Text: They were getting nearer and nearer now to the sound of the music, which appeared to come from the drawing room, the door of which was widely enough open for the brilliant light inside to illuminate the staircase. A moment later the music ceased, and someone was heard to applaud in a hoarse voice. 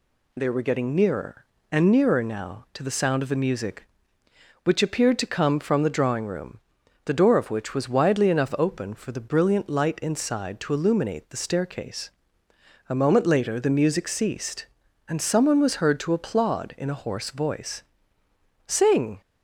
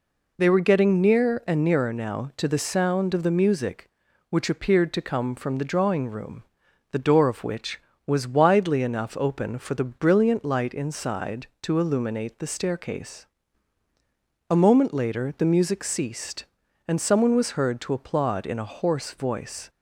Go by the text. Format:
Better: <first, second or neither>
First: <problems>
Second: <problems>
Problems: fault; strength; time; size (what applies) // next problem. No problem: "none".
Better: second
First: goes on to say "Sing"; from 18.6 s on; 0.54 s long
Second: none